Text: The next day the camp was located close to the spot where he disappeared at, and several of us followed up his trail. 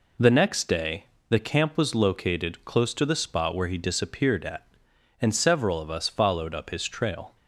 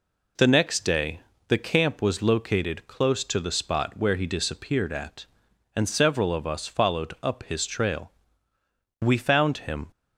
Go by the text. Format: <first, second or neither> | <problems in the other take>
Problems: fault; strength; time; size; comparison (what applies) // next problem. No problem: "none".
first | pauses between "day" and "the"; slight; at 1.2 s; 0.26 s long; slight in the first // goes on to say "We found him"; noticeable; from 9.0 s on; 0.86 s long